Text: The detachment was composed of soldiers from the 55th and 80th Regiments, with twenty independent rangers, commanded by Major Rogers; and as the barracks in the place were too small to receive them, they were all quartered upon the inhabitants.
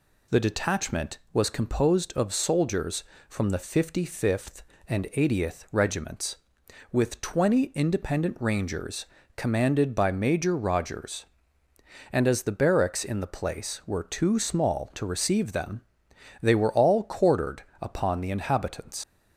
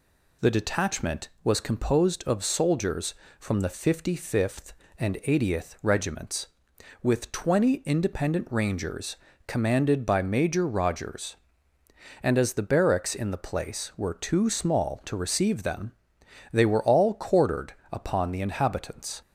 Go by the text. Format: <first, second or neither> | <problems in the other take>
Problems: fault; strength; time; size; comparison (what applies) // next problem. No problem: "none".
second | pauses between "quartered" and "upon"; slight; at 17.6 s; 0.18 s long; slight in the second // leaves "inhabitants" unfinished; at 19.0 s; 65 ms